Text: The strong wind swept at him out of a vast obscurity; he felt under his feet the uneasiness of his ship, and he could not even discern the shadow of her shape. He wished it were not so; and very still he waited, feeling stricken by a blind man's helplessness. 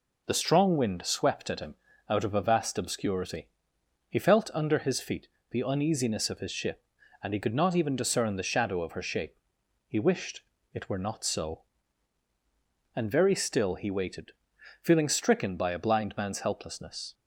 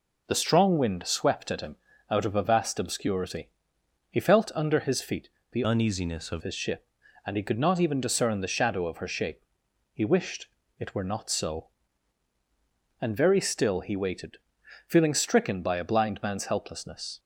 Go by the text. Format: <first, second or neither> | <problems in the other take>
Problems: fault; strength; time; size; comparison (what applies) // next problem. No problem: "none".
first | pauses between "him" and "out"; slight; at 1.7 s; 0.34 s long; slight in the first // pauses between "feet" and "the"; slight; at 5.2 s; 0.24 s long; slight in the first // changes voice from "uneasiness" to "of"; from 5.6 to 6.4 s; 0.8 s long // pauses between "wished" and "it"; slight; at 10.4 s; 0.32 s long; slight in the first